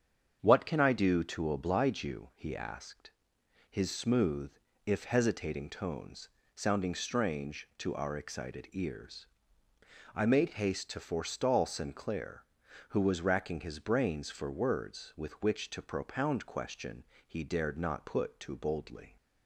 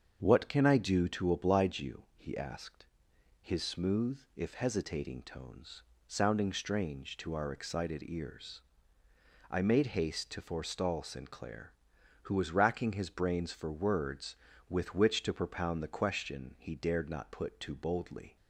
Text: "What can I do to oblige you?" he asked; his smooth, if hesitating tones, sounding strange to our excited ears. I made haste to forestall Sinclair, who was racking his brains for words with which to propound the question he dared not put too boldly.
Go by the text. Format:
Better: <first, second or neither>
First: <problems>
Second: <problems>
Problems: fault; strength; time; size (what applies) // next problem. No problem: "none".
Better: second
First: starts louder than the rest; strong; until 1.4 s; 7.5 dB // skips "the"; at 16.4 s // pauses between "question" and "he"; slight; at 17.0 s; 0.20 s long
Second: starts louder than the rest; until 1.2 s; 7 dB